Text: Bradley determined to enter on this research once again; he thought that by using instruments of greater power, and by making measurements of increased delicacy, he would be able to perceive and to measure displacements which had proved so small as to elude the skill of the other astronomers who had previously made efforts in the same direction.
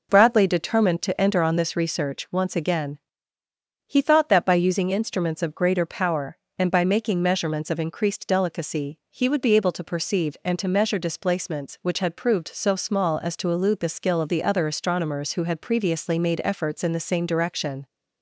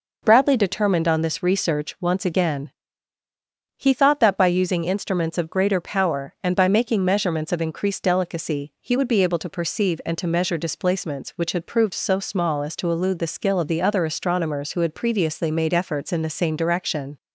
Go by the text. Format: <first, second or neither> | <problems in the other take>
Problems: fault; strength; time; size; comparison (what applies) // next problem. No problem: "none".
first | skips "to enter"; at 1.0 s